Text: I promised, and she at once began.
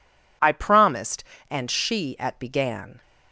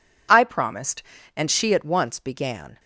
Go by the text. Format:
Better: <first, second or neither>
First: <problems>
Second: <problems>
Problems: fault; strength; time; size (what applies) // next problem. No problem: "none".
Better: second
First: skips "once"; at 2.3 s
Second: none